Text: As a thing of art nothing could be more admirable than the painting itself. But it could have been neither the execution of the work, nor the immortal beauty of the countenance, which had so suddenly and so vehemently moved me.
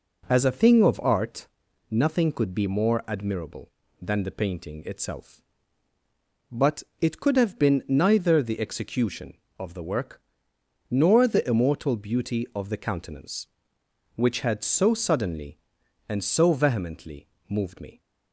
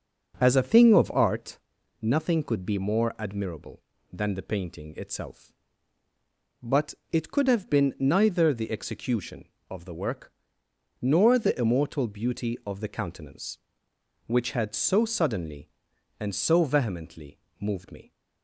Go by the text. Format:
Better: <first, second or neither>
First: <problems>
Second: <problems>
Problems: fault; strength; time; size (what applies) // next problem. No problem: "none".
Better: first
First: pauses between "art" and "nothing"; at 1.4 s; 0.44 s long // pauses between "But" and "it"; slight; at 6.8 s; 0.18 s long // pauses between "vehemently" and "moved"; slight; at 17.2 s; 0.22 s long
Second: starts louder than the rest; noticeable; until 1.4 s; 6 dB // pauses between "art" and "nothing"; at 1.5 s; 0.44 s long // pauses between "But" and "it"; slight; at 6.9 s; 0.18 s long // pauses between "vehemently" and "moved"; slight; at 17.3 s; 0.22 s long